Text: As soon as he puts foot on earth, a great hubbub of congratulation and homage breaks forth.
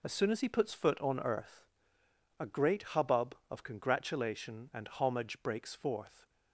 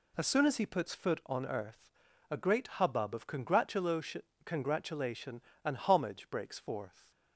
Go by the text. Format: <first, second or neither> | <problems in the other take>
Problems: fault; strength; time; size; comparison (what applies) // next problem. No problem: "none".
first | says "congratulation" twice; at 4.4 s